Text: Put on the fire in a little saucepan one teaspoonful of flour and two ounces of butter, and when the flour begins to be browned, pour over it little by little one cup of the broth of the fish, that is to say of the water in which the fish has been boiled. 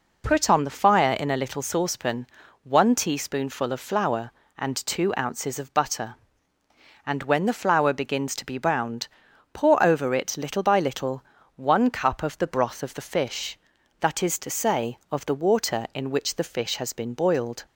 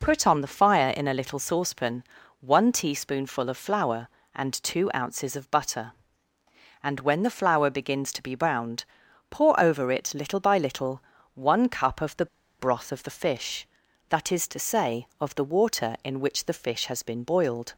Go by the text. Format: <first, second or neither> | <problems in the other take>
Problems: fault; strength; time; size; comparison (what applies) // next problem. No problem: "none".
first | pauses between "saucepan" and "one"; at 2.0 s; 0.38 s long; also in the first // pauses between "little" and "one"; slight; at 11.0 s; 0.36 s long; slight in the first // pauses between "the" and "broth"; slight; at 12.2 s; 0.33 s long